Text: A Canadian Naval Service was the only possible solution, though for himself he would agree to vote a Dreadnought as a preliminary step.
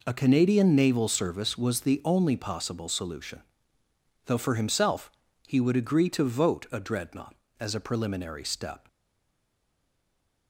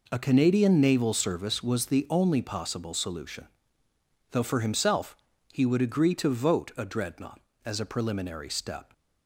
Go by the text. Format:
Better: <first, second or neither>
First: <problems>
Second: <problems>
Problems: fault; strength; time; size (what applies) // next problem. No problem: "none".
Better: second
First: pauses between "himself" and "he"; slight; at 5.1 s; 0.34 s long // stays silent after the last word; noticeable; from 8.8 s on; 1.6 s long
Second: pauses between "himself" and "he"; slight; at 5.1 s; 0.34 s long